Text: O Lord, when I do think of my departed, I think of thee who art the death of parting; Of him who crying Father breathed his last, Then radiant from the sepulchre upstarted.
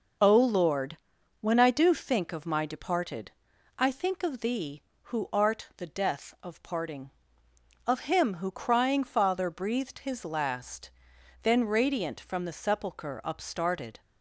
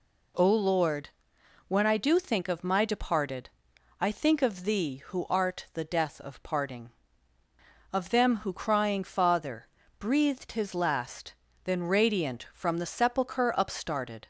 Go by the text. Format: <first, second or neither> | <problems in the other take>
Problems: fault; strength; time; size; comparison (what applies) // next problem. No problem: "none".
first | says "them" for "him"; at 8.0 s // pauses between "Father" and "breathed"; slight; at 9.6 s; 0.28 s long